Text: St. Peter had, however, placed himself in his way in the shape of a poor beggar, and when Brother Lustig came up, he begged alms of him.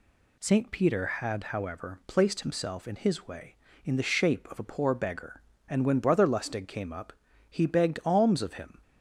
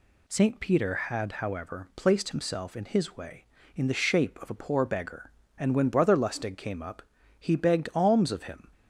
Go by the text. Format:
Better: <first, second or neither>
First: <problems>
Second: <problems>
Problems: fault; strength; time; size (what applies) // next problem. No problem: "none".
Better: neither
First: none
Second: none